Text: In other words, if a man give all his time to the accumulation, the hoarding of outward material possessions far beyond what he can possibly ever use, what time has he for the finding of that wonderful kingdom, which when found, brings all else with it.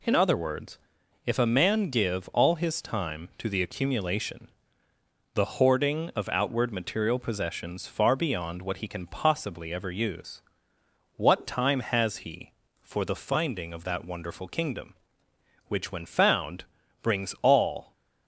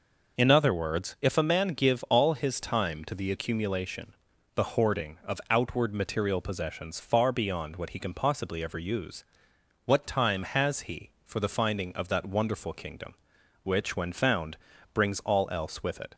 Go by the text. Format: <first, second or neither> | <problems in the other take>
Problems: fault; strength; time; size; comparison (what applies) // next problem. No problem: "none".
second | stops before "else with it"; at 17.9 s